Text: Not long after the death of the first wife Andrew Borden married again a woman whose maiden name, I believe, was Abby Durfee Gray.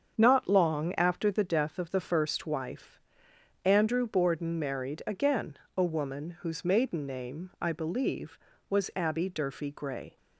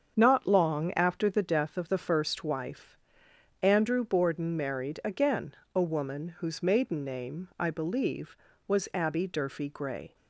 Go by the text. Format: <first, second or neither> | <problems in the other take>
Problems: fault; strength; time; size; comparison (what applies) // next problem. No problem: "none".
neither | starts louder than the rest; strong; the same in both // pauses between "wife" and "Andrew"; noticeable; the same in both // pauses between "again" and "a"; slight; the same in both